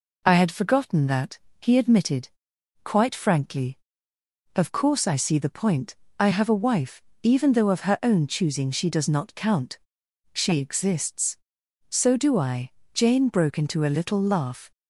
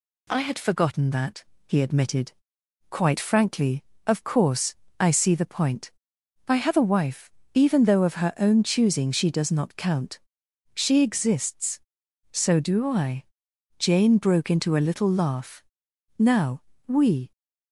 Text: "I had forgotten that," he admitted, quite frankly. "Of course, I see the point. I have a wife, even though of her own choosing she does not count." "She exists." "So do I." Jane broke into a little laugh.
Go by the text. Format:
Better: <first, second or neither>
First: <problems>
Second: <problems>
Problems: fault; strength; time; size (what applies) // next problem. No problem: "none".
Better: first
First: none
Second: goes on to say "Now we"; noticeable; from 16.1 s on; 1.1 s long